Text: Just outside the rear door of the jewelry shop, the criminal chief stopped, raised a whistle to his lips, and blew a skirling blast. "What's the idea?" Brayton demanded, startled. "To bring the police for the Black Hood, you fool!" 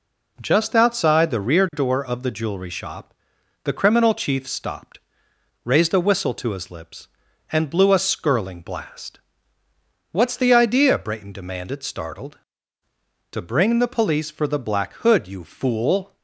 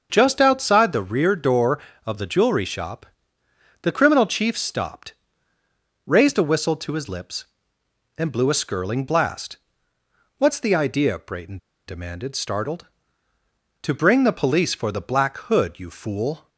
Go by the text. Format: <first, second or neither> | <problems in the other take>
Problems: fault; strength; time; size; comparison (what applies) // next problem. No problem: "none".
first | starts louder than the rest; until 1.1 s; 6.5 dB // pauses between "Brayton" and "demanded"; slight; at 11.5 s; 0.30 s long